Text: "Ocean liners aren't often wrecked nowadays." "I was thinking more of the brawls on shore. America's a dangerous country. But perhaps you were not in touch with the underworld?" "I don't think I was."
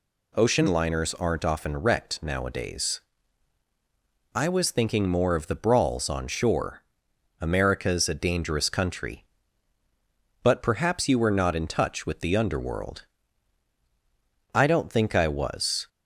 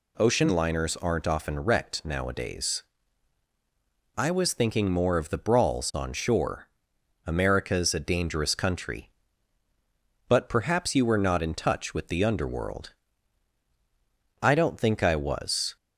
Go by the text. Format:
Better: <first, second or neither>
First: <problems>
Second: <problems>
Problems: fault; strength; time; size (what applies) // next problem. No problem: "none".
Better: neither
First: none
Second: none